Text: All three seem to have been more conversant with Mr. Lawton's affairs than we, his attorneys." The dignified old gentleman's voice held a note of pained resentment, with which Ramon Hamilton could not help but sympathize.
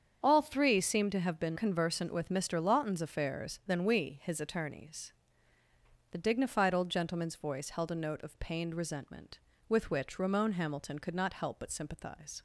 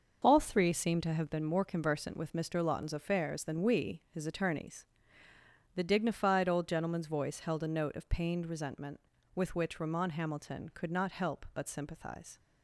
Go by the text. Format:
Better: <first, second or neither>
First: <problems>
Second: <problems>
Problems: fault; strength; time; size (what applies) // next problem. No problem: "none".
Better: second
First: starts louder than the rest; strong; until 1.2 s; 7.5 dB // skips "more"; at 1.5 s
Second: starts louder than the rest; until 1.2 s; 6 dB